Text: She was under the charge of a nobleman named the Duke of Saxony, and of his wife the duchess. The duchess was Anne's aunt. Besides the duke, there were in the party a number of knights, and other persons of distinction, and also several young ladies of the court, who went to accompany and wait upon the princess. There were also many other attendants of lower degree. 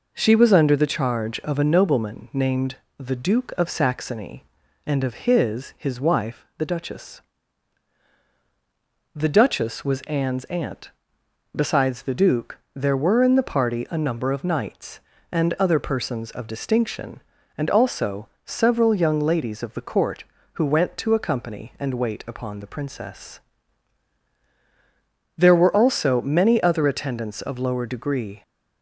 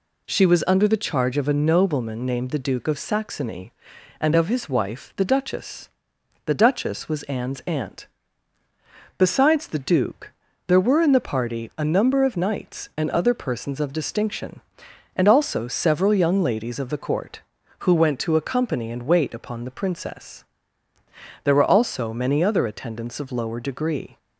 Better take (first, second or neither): second